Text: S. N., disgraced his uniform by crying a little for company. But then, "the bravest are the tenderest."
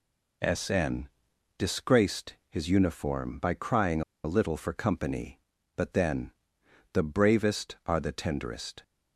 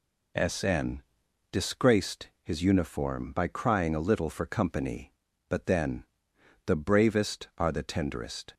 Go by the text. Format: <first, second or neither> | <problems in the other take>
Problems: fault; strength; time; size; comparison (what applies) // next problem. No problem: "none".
second | pauses between "disgraced" and "his"; slight; at 2.3 s; 0.16 s long; slight in the second // pauses between "crying" and "a"; slight; at 4.0 s; 0.22 s long